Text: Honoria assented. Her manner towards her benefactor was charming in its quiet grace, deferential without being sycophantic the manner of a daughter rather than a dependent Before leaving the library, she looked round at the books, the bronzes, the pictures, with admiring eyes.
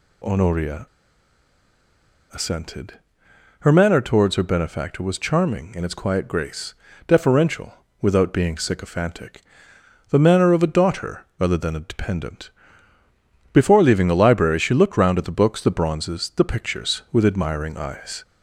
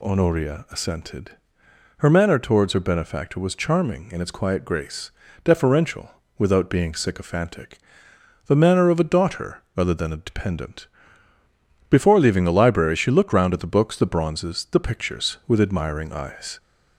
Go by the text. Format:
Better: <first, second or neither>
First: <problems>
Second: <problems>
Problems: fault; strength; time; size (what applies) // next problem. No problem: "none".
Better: second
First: pauses between "Honoria" and "assented"; strong; at 0.8 s; 1.4 s long // pauses between "deferential" and "without"; slight; at 7.7 s; 0.30 s long // pauses between "sycophantic" and "the"; noticeable; at 9.4 s; 0.68 s long // pauses between "daughter" and "rather"; slight; at 11.2 s; 0.16 s long // pauses between "dependent" and "Before"; at 12.4 s; 1.0 s long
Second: pauses between "deferential" and "without"; slight; at 6.0 s; 0.30 s long // pauses between "sycophantic" and "the"; noticeable; at 7.7 s; 0.68 s long // pauses between "daughter" and "rather"; slight; at 9.6 s; 0.16 s long // pauses between "dependent" and "Before"; at 10.8 s; 1.0 s long